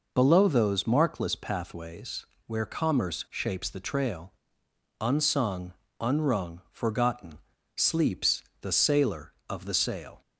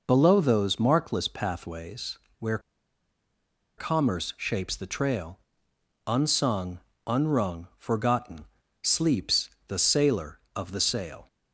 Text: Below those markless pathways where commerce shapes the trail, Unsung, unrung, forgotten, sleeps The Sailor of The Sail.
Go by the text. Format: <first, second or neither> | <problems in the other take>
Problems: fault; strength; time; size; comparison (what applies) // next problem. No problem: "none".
first | pauses between "pathways" and "where"; slight; at 2.1 s; 0.18 s long; slight in the first // pauses between "where" and "commerce"; at 2.5 s; 1.1 s long // pauses between "sleeps" and "The"; slight; at 9.5 s; 0.16 s long; slight in the first